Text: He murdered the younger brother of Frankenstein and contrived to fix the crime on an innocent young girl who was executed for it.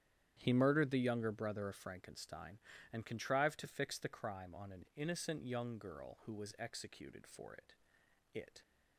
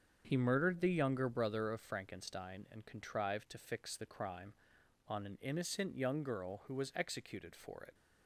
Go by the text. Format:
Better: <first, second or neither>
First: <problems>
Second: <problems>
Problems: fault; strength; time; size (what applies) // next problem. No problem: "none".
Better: second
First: starts louder than the rest; strong; until 1.4 s; 10 dB // says "it" twice; at 8.3 s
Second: starts louder than the rest; strong; until 1.2 s; 7 dB